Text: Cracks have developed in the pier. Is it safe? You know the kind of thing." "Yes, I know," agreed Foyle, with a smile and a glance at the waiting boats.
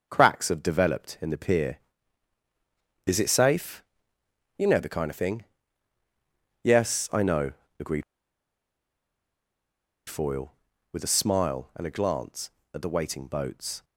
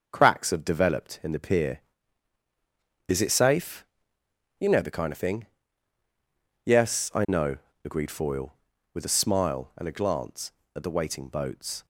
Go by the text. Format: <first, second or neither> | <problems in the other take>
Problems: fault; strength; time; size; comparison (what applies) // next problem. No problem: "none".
second | starts louder than the rest; until 1.1 s; 6 dB; also in the second // pauses between "agreed" and "Foyle"; strong; at 8.0 s; 2.0 s long